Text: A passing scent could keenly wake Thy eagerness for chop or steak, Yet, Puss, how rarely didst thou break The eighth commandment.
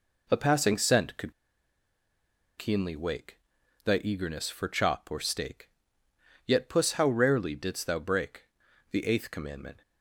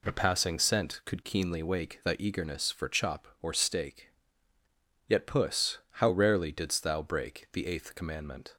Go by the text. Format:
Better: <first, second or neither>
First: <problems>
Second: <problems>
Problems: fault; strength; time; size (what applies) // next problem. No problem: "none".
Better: second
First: pauses between "could" and "keenly"; strong; at 1.3 s; 1.2 s long // pauses between "wake" and "Thy"; noticeable; at 3.3 s; 0.46 s long // pauses between "break" and "The"; noticeable; at 8.4 s; 0.48 s long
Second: none